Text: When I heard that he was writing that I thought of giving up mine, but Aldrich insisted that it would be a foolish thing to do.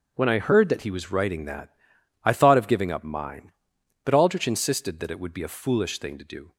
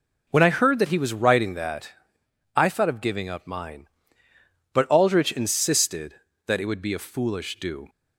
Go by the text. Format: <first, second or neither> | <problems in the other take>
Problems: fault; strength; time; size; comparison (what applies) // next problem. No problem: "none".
first | pauses between "that" and "I"; noticeable; at 1.9 s; 0.62 s long; noticeable in the first // skips "thing to"; at 7.5 s